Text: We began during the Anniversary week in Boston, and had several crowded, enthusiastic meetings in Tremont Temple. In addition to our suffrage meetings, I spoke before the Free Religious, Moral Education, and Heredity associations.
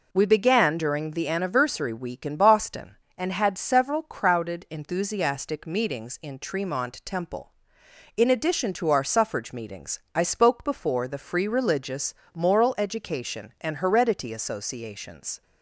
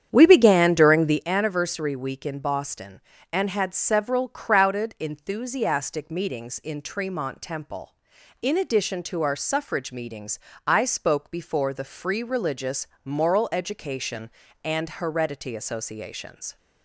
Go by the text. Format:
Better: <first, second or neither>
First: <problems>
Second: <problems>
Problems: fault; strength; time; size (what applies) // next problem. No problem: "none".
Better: first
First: none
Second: starts louder than the rest; strong; until 1.2 s; 9 dB